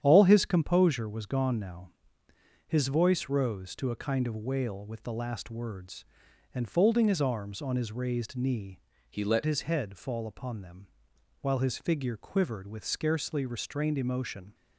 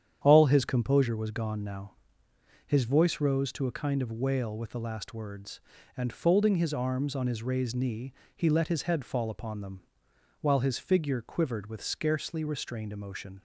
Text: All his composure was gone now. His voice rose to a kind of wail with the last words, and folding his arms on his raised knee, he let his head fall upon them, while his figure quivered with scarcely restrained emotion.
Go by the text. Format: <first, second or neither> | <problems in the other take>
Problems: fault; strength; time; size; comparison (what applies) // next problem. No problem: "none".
second | starts louder than the rest; strong; until 1.0 s; 9.5 dB; strong in the second // changes voice from "he" to "let"; from 9.1 to 9.4 s; 0.3 s long